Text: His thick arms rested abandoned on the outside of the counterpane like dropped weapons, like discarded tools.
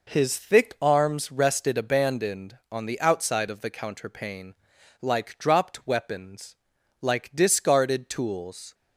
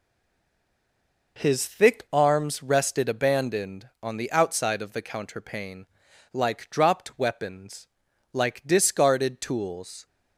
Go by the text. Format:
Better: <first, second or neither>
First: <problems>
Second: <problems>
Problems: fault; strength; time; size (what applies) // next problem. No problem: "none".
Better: first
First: pauses between "counterpane" and "like"; noticeable; at 4.5 s; 0.48 s long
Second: stays silent before the first word; noticeable; until 1.3 s; 1.3 s long // pauses between "counterpane" and "like"; noticeable; at 5.8 s; 0.48 s long